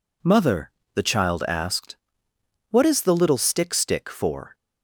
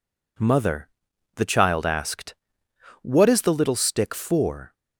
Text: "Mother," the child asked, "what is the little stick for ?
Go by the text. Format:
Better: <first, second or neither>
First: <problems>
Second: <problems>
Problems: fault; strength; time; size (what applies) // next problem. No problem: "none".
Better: second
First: says "stick" twice; at 3.7 s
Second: none